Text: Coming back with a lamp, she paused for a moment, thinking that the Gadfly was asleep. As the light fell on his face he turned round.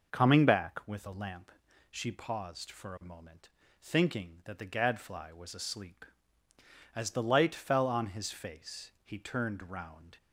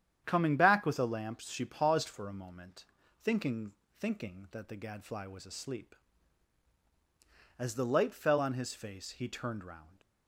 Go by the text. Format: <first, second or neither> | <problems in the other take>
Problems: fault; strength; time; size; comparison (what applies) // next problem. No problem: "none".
first | starts louder than the rest; strong; until 1.2 s; 9.5 dB // says "thinking" twice; at 4.0 s